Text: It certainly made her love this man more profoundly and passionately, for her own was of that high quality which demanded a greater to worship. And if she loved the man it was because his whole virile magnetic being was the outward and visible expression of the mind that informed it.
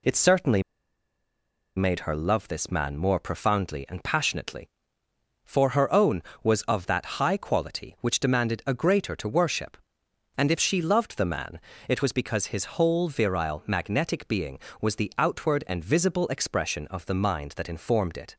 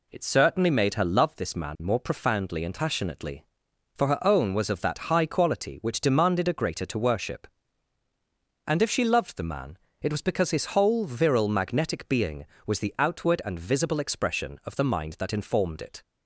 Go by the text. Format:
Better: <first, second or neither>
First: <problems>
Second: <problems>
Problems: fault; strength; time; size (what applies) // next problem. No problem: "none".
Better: second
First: pauses between "certainly" and "made"; at 0.6 s; 1.1 s long // pauses between "man" and "it"; slight; at 11.5 s; 0.30 s long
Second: pauses between "man" and "it"; slight; at 9.7 s; 0.26 s long